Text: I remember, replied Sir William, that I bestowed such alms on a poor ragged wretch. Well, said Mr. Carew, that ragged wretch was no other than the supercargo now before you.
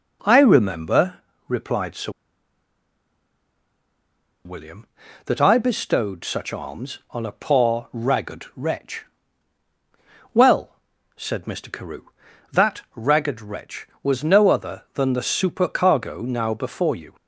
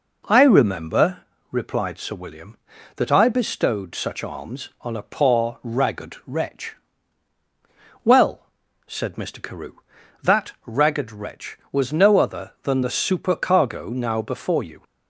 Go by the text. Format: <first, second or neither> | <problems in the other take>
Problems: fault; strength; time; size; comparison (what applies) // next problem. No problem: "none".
second | pauses between "Sir" and "William"; strong; at 2.1 s; 2.3 s long